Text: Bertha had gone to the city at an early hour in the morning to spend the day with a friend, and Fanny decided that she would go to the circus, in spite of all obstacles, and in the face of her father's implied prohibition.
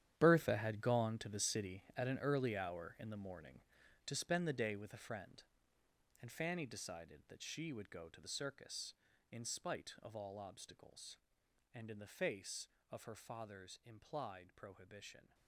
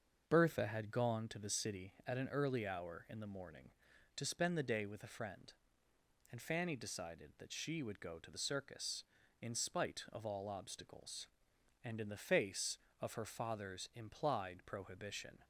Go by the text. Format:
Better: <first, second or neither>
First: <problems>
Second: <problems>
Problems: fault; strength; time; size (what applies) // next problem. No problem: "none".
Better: second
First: gets quieter; strong; throughout; 13 dB // starts louder than the rest; strong; until 1.1 s; 10.5 dB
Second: starts louder than the rest; until 1.2 s; 6.5 dB